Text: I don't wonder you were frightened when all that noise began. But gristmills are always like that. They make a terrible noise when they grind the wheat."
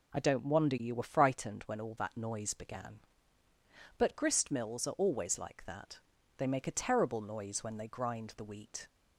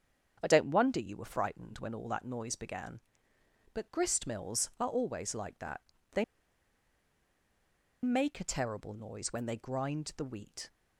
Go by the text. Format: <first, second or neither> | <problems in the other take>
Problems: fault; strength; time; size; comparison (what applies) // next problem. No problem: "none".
first | starts louder than the rest; strong; until 1.4 s; 7.5 dB // pauses between "They" and "make"; strong; at 6.2 s; 1.7 s long